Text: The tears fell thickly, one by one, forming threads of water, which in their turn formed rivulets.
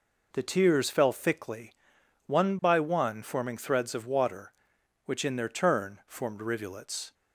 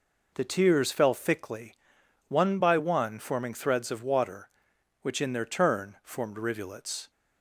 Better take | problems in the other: neither | none

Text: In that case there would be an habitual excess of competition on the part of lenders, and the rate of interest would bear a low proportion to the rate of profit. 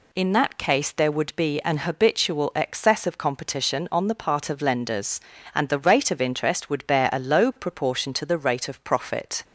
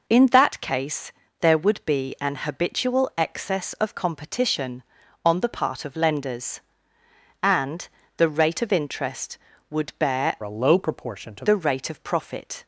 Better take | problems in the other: first | pauses between "case" and "there"; slight; at 1.1 s; 0.30 s long // pauses between "and" and "the"; slight; at 7.8 s; 0.30 s long // changes voice from "a" to "to"; from 10.4 to 11.4 s; 1.0 s long

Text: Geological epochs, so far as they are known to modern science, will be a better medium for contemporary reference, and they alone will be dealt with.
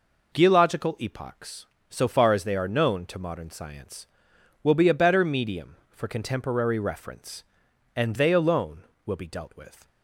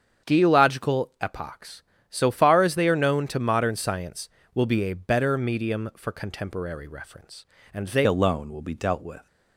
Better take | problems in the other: first | starts louder than the rest; strong; until 1.3 s; 8 dB // changes voice at "alone"; from 8.0 s on; 1.2 s long

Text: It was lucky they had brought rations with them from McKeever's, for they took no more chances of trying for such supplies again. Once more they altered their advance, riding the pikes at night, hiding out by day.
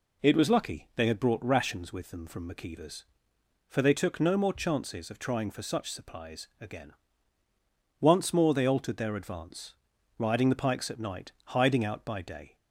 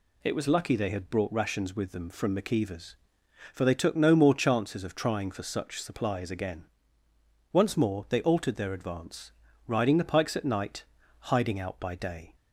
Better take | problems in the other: neither | none

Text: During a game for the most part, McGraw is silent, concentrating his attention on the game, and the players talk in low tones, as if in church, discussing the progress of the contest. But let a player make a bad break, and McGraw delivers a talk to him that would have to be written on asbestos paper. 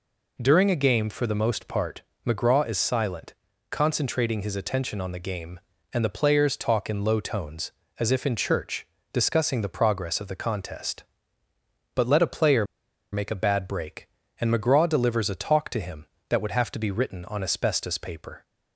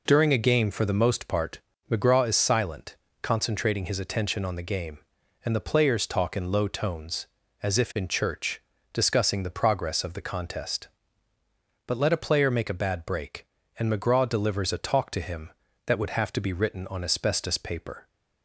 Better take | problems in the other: second | pauses between "player" and "make"; noticeable; at 12.6 s; 0.47 s long

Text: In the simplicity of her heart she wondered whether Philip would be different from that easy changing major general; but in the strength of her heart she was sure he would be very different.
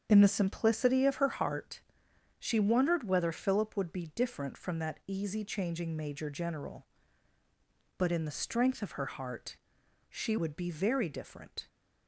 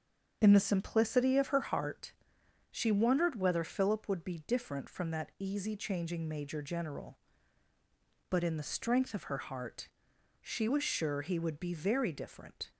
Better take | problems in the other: second | starts louder than the rest; strong; until 1.1 s; 7.5 dB; strong in the second // pauses between "heart" and "she"; noticeable; at 1.7 s; 0.58 s long; noticeable in the second // pauses between "heart" and "she"; noticeable; at 9.5 s; 0.54 s long; noticeable in the second // skips "was sure he"; at 10.3 s

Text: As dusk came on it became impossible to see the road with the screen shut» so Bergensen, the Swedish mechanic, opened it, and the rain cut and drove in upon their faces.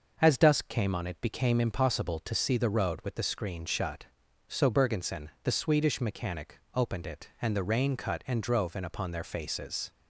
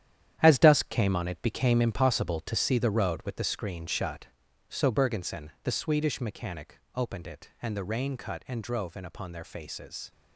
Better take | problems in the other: first | gets quieter; strong; throughout; 9.5 dB // starts louder than the rest; strong; until 1.4 s; 10.5 dB; noticeable in the first

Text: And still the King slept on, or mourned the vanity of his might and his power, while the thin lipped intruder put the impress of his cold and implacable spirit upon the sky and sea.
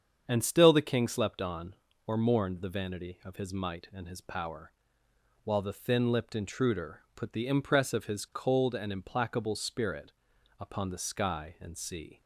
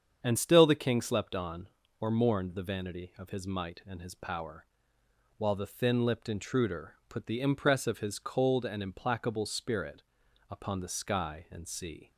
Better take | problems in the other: neither | starts louder than the rest; strong; the same in both // pauses between "spirit" and "upon"; noticeable; the same in both

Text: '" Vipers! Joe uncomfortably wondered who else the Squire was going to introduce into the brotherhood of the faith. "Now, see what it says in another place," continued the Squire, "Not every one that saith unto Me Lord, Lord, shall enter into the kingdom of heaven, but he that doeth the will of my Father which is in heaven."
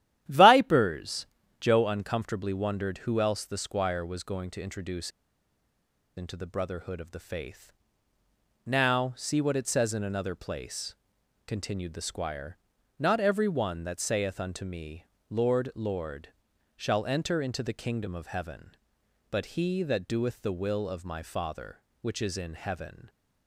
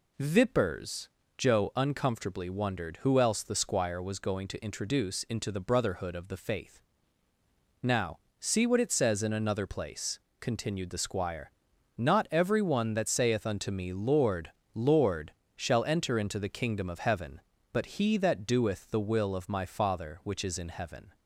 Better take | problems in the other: second | starts louder than the rest; strong; until 1.6 s; 12 dB // pauses between "introduce" and "into"; at 5.0 s; 1.0 s long // pauses between "Me" and "Lord"; slight; at 15.0 s; 0.26 s long

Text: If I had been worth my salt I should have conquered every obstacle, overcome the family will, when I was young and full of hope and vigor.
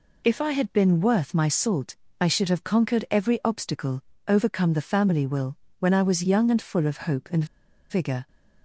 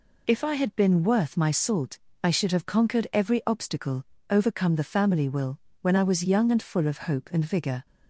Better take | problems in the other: second | pauses between "salt" and "I"; slight; at 1.9 s; 0.26 s long; slight in the second // pauses between "and" and "vigor"; at 7.4 s; 0.45 s long

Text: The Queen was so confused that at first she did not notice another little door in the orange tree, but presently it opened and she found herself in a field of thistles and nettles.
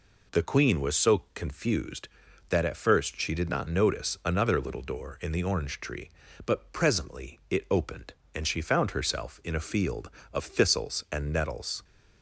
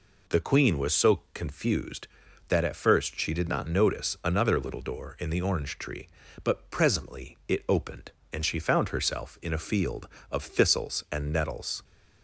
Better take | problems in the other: neither | none

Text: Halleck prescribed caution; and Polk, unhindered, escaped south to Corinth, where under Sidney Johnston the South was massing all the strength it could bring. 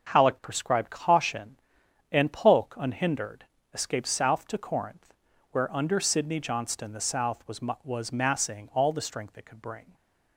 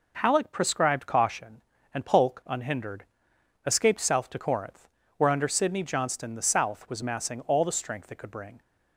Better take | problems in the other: second | starts louder than the rest; strong; until 1.1 s; 7.5 dB // says "was" twice; at 7.8 s

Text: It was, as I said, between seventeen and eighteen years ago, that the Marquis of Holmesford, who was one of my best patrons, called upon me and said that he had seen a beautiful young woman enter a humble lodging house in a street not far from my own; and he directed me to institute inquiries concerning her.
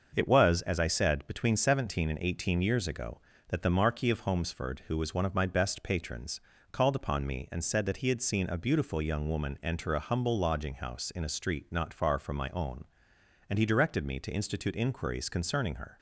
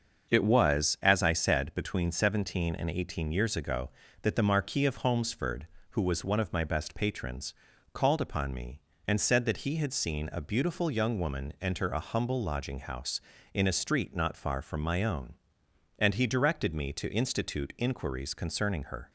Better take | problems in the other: neither | starts louder than the rest; the same in both

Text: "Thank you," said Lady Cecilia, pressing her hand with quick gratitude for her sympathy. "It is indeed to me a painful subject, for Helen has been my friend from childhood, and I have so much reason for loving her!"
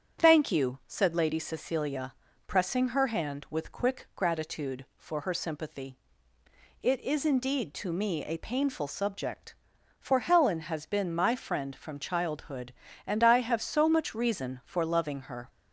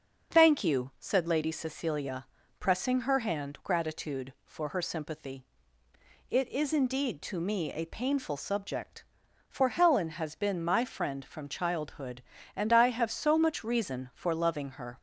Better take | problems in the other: first | starts louder than the rest; noticeable; until 1.3 s; 6 dB; strong in the first // skips "with quick"; at 3.6 s

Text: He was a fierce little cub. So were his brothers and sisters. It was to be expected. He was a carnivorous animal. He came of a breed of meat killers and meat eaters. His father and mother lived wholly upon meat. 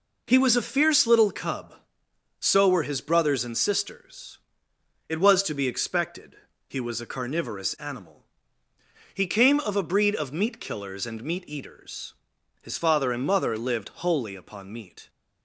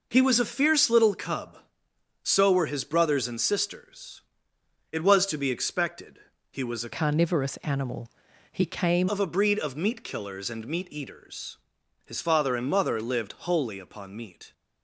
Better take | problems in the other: first | changes voice from "carnivorous" to "came"; from 6.9 to 9.0 s; 2.1 s long

